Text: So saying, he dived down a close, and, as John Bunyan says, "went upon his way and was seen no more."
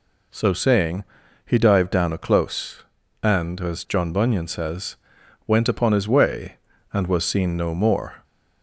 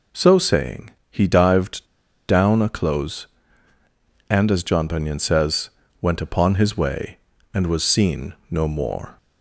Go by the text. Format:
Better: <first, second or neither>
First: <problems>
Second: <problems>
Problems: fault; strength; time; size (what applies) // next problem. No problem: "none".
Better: first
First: none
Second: pauses between "dived" and "down"; at 1.8 s; 0.43 s long // pauses between "seen" and "no"; slight; at 8.3 s; 0.16 s long